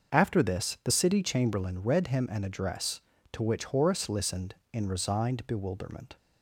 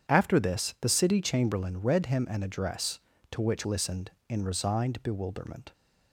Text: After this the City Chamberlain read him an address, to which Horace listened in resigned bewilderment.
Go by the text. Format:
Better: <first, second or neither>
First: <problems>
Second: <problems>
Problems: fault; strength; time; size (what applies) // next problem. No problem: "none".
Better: first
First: starts louder than the rest; until 1.1 s; 6.5 dB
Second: starts louder than the rest; strong; until 1.1 s; 8.5 dB // skips "Horace"; at 3.6 s